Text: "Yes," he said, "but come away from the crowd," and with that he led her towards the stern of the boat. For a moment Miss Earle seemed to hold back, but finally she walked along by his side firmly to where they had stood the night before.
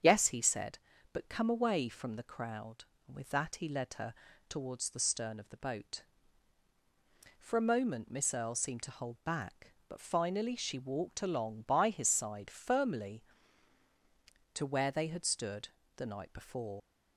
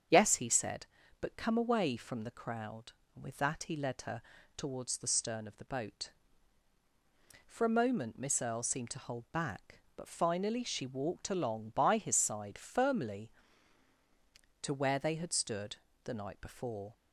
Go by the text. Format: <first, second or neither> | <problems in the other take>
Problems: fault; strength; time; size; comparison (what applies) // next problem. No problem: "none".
second | starts louder than the rest; strong; until 1.3 s; 7.5 dB; strong in the second // pauses between "her" and "towards"; slight; at 4.1 s; 0.34 s long; slight in the second // pauses between "stood" and "the"; slight; at 15.6 s; 0.26 s long; slight in the second // leaves "before" unfinished; at 16.7 s; 50 ms